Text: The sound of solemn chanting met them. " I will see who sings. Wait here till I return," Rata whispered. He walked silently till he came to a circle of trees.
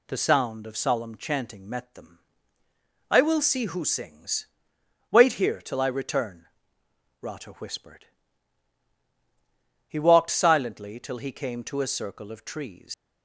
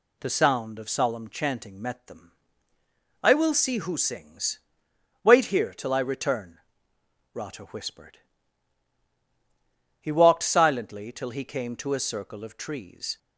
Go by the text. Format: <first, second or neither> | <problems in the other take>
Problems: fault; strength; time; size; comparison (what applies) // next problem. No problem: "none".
second | leaves "trees" unfinished; at 12.9 s; 115 ms